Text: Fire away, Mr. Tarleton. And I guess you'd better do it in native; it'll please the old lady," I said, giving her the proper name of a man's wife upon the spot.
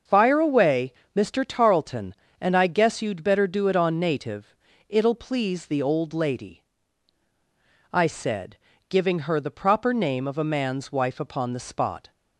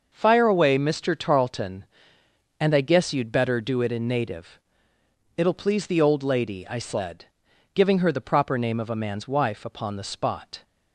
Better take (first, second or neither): second